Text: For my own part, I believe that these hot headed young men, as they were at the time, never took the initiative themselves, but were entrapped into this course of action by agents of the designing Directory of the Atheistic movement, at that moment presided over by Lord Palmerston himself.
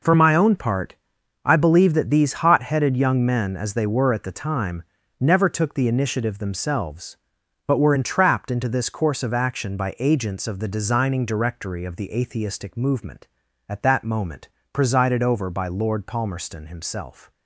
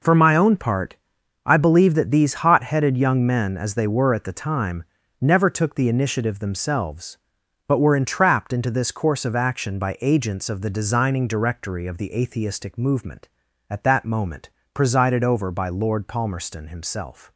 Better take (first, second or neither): neither